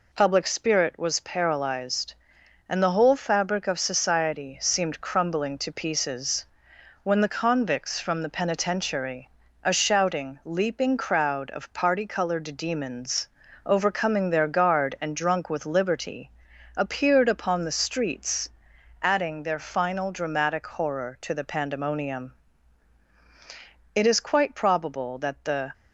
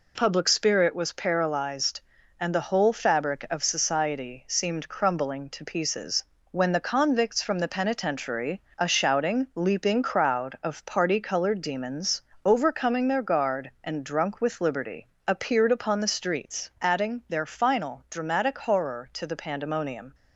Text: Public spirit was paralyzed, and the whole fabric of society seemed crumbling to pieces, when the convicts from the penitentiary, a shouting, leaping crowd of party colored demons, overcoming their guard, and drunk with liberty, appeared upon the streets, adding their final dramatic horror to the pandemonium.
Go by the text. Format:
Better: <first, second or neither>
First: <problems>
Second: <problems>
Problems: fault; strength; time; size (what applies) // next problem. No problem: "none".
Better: second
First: goes on to say "It is quite probable that the"; strong; from 23.9 s on; 1.7 s long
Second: none